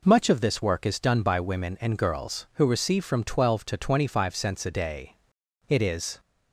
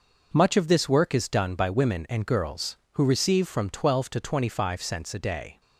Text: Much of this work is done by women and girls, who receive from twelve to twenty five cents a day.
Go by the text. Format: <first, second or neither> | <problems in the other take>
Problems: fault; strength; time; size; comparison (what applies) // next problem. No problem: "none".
second | goes on to say "It is"; from 5.6 s on; 0.50 s long